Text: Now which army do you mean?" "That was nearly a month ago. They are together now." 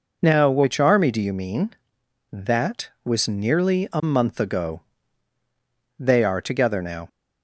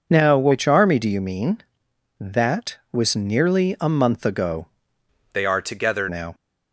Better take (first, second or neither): first